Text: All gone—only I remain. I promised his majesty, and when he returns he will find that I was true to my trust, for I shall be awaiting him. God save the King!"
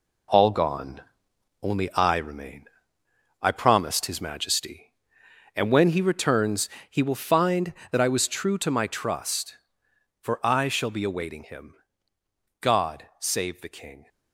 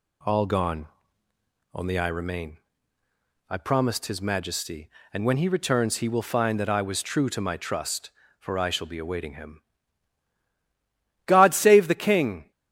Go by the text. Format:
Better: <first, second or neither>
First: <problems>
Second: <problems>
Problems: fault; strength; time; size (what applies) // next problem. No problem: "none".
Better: second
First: gets quieter; throughout; 6.5 dB // pauses between "returns" and "he"; slight; at 6.6 s; 0.18 s long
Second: none